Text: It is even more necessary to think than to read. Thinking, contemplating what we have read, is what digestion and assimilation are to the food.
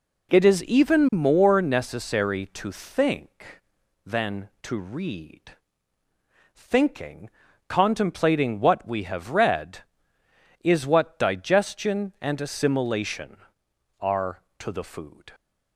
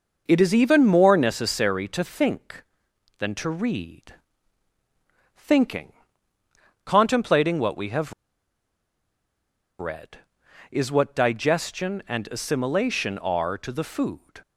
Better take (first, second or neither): first